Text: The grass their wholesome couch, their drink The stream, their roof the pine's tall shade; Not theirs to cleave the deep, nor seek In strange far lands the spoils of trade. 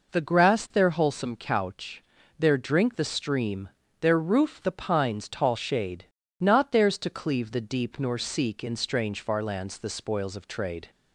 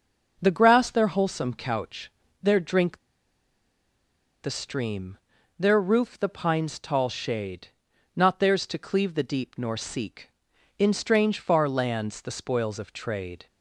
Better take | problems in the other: first | pauses between "drink" and "The"; strong; at 2.9 s; 1.4 s long

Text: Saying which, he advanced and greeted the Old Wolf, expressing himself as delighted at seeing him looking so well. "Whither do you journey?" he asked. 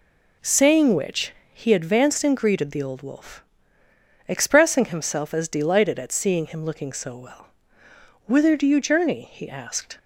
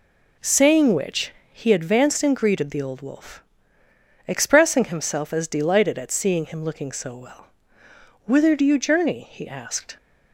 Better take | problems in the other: neither | none

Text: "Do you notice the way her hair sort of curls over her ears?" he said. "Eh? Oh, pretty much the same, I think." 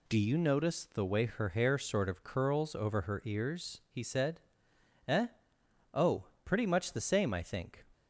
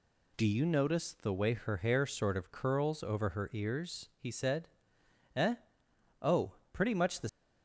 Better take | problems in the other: first | stops before "same I think"; at 7.2 s

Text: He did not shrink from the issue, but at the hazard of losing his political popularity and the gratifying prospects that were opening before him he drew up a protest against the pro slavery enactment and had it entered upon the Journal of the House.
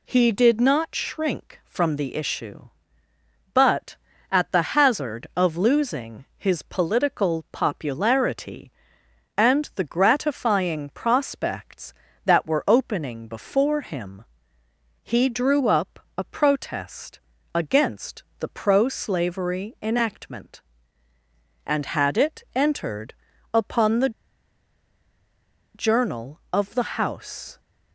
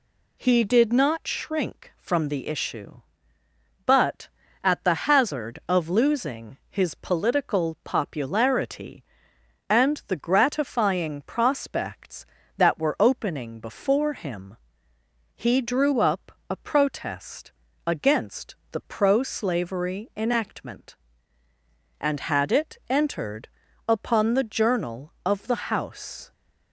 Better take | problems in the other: second | pauses between "the" and "hazard"; slight; at 4.6 s; 0.16 s long; slight in the second // pauses between "him" and "he"; noticeable; at 14.2 s; 0.80 s long; noticeable in the second // pauses between "up" and "a"; slight; at 15.9 s; 0.18 s long; slight in the second // pauses between "protest" and "against"; slight; at 17.1 s; 0.34 s long; slight in the second // pauses between "against" and "the"; slight; at 18.2 s; 0.16 s long; slight in the second // pauses between "entered" and "upon"; at 23.1 s; 0.40 s long; also in the second // pauses between "the" and "Journal"; strong; at 24.0 s; 1.6 s long

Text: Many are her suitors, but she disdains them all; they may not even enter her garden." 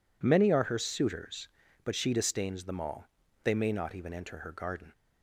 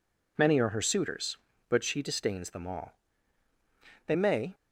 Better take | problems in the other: first | stops before "not even enter her garden"; at 4.5 s

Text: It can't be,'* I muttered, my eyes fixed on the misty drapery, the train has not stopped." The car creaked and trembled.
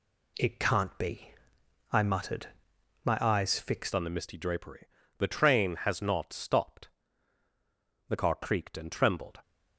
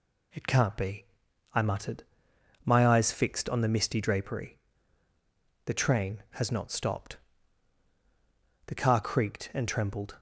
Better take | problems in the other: second | changes voice at "on"; from 3.9 s on; 5.5 s long

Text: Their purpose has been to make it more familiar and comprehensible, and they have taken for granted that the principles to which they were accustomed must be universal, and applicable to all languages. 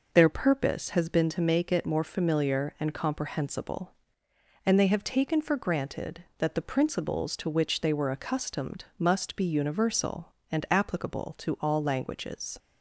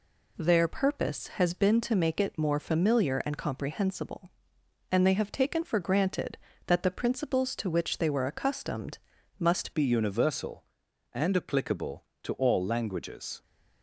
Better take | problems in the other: first | pauses between "accustomed" and "must"; at 8.9 s; 0.40 s long // changes voice at "be"; from 9.7 s on; 3.7 s long

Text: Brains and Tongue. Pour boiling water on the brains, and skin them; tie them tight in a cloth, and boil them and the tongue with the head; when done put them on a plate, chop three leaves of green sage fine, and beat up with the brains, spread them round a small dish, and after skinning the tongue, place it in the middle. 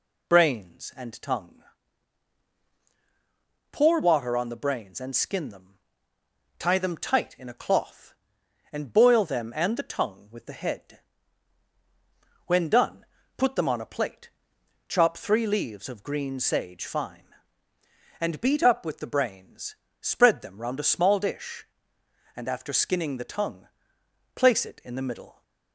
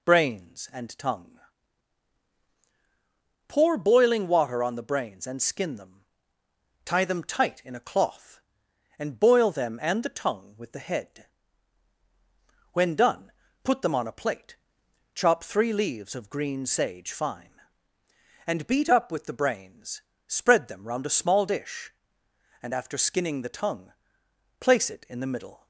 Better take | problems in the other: second | skips "boiling"; at 4.0 s // pauses between "done" and "put"; slight; at 13.0 s; 0.32 s long; slight in the second

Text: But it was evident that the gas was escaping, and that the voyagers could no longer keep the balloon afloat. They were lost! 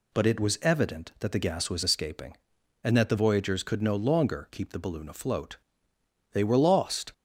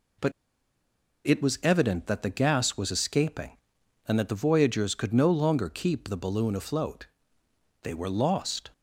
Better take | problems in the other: first | pauses between "But" and "it"; noticeable; at 0.3 s; 0.95 s long

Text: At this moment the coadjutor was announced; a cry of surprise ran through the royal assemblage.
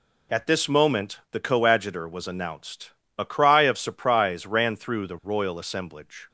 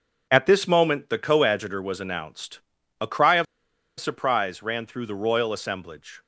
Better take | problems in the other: first | pauses between "of" and "surprise"; noticeable; at 3.4 s; 0.55 s long

